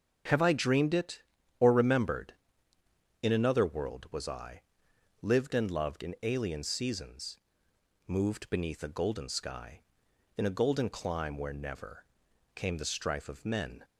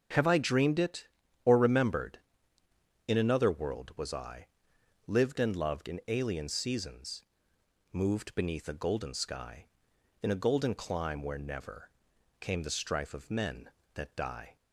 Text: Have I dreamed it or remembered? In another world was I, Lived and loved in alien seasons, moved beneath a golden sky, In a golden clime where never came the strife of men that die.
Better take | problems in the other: second | starts louder than the rest; strong; until 1.6 s; 7.5 dB; strong in the second // pauses between "never" and "came"; noticeable; at 12.0 s; 0.50 s long; noticeable in the second // stops before "that die"; at 13.8 s

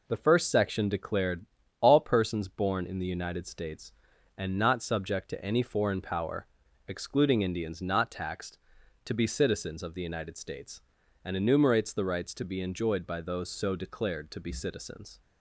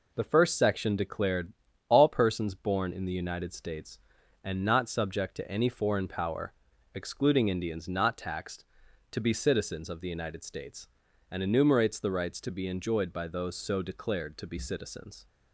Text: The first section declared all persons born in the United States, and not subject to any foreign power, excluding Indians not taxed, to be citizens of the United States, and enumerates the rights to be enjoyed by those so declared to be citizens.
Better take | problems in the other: neither | pauses between "declared" and "all"; slight; the same in both

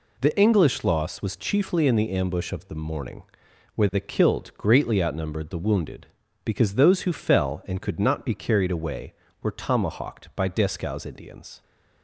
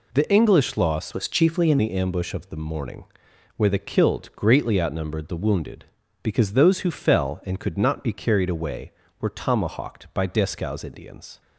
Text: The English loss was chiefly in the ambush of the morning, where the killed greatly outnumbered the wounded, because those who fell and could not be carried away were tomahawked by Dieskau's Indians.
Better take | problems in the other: first | changes voice from "was" to "in"; from 1.1 to 1.7 s; 0.6 s long

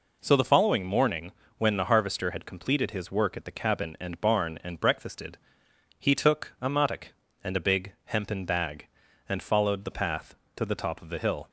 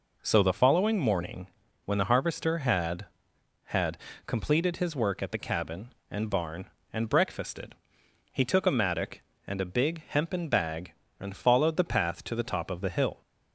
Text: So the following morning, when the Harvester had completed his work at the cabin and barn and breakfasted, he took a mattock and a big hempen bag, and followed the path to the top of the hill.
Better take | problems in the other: first | says "had" twice; at 3.6 s

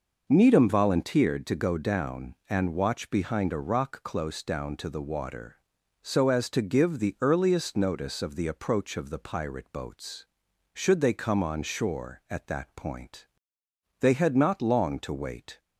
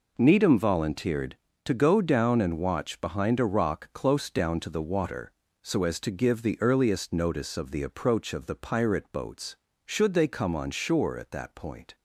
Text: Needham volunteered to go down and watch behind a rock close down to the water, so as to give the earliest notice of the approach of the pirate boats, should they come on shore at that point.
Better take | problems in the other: second | goes on to say "They had not long to wait"; from 13.9 s on; 1.6 s long

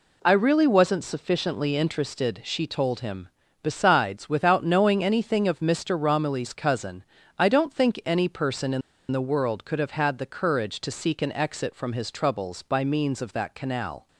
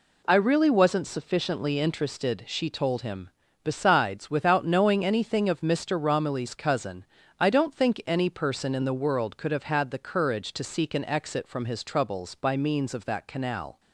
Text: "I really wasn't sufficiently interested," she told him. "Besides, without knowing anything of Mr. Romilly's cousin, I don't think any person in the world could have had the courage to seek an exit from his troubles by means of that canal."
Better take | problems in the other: second | pauses between "in" and "the"; slight; at 8.8 s; 0.30 s long

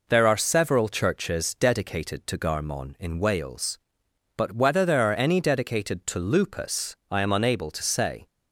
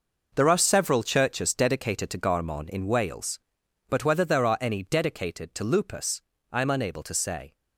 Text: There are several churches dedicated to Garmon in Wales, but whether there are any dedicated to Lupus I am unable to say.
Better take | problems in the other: first | gets quieter; strong; throughout; 10 dB // pauses between "Lupus" and "I"; slight; at 6.2 s; 0.30 s long; slight in the first

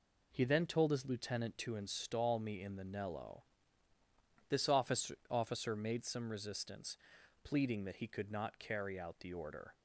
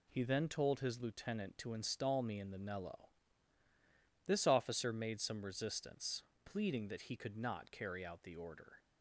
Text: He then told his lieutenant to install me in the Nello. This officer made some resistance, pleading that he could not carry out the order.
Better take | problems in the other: second | says "officer" twice; at 5.2 s

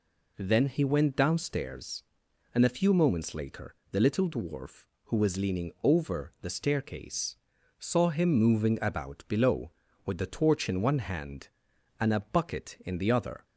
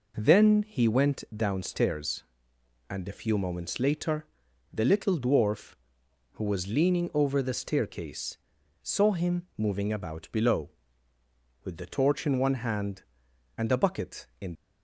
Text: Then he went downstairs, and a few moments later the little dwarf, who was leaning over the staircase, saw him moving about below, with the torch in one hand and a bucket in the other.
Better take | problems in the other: first | pauses between "later" and "the"; noticeable; at 4.2 s; 0.46 s long; slight in the first // stops before "the other"; at 14.5 s

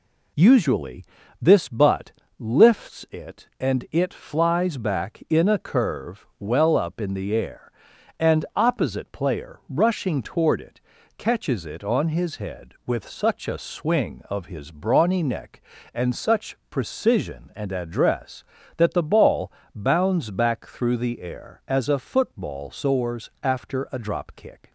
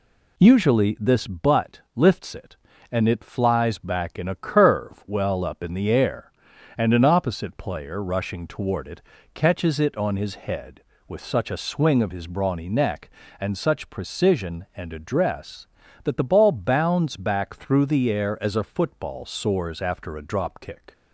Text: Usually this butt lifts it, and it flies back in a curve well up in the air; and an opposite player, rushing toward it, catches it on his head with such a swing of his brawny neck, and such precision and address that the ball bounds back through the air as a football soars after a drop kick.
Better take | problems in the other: second | pauses between "Usually" and "this"; slight; at 1.0 s; 0.36 s long // pauses between "butt" and "lifts"; slight; at 2.1 s; 0.28 s long // skips "an"; at 8.4 s // pauses between "ball" and "bounds"; slight; at 19.5 s; 0.24 s long

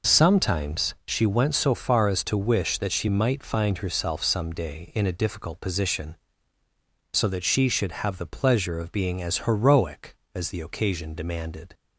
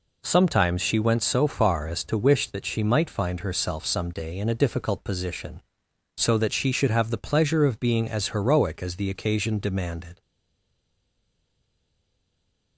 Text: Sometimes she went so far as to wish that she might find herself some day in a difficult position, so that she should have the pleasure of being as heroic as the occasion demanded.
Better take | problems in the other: first | stays silent after the last word; strong; from 10.2 s on; 2.5 s long

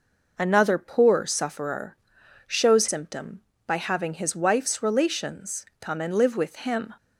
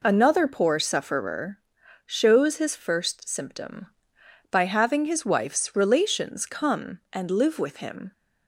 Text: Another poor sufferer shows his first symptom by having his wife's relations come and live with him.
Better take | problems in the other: second | pauses between "sufferer" and "shows"; noticeable; at 1.9 s; 0.50 s long; noticeable in the second // skips "his first"; at 2.8 s

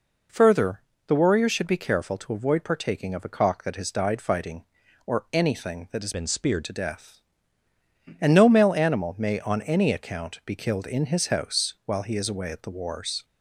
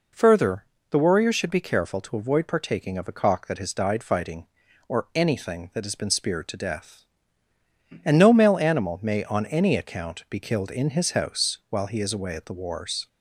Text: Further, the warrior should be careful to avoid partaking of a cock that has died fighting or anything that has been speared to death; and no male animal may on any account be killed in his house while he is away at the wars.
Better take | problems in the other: second | changes voice from "been" to "speared"; from 6.1 to 6.6 s; 0.5 s long

